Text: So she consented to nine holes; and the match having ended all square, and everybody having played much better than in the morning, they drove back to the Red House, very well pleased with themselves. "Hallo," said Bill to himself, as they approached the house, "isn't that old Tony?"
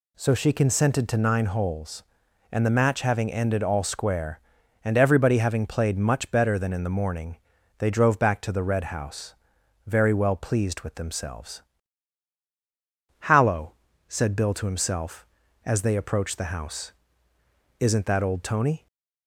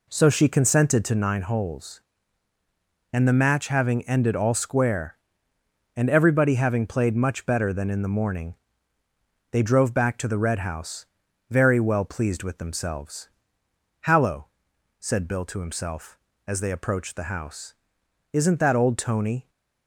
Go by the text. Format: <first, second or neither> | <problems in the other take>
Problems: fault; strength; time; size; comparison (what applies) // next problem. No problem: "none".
first | starts louder than the rest; slight; until 1.3 s; 3 dB